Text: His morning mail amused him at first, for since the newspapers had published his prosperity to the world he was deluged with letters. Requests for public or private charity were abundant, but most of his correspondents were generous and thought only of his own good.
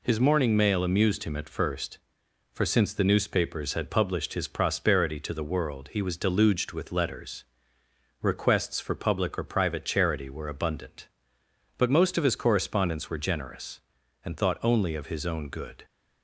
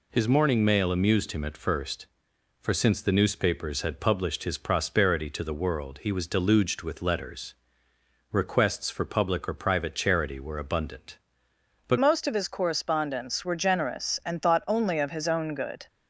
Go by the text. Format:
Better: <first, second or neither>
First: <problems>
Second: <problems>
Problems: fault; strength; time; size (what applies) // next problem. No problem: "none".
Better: first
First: none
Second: changes voice at "most"; from 11.9 s on; 3.9 s long